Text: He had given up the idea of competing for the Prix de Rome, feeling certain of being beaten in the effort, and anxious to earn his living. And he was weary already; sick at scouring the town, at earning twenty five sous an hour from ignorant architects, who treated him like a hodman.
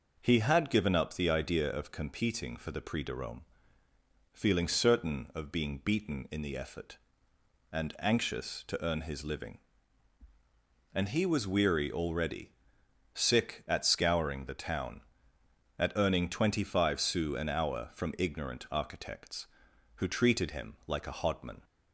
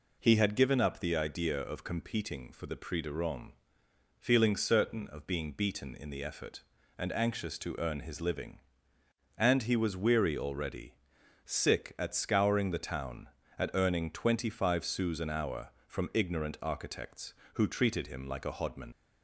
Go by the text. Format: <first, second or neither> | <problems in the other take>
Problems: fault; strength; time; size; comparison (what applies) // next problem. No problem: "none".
first | leaves "hodman" unfinished; at 18.9 s; 75 ms